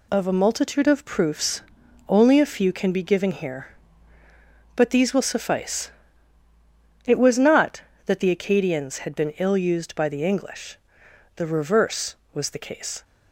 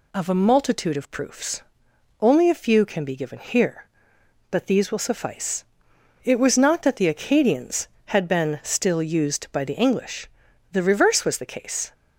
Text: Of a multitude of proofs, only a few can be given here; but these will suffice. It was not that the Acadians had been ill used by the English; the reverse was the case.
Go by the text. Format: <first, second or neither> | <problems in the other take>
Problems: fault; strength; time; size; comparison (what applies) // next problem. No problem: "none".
first | says "still" for "ill"; at 8.6 s